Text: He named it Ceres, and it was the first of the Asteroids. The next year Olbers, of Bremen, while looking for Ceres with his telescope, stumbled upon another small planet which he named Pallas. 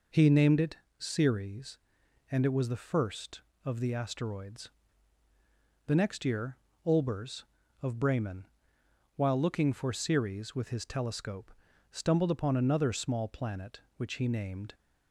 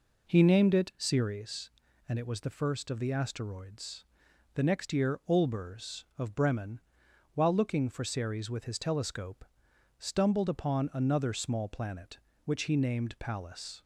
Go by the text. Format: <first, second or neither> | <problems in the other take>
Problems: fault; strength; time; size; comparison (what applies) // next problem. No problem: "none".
second | pauses between "it" and "Ceres"; slight; at 0.7 s; 0.24 s long // pauses between "year" and "Olbers"; slight; at 6.5 s; 0.30 s long // stops before "Pallas"; at 14.7 s